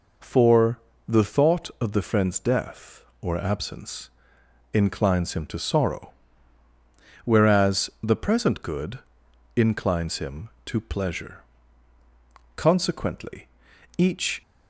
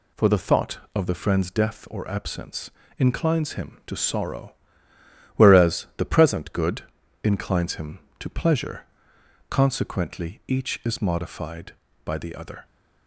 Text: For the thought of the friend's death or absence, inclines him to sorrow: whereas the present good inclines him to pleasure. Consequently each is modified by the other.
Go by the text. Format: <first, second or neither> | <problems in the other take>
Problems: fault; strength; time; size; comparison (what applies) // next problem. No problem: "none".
second | pauses between "For" and "the"; slight; at 0.7 s; 0.28 s long // pauses between "good" and "inclines"; noticeable; at 8.9 s; 0.56 s long; also in the second // pauses between "Consequently" and "each"; noticeable; at 13.4 s; 0.50 s long // stops before "is modified by the other"; at 14.4 s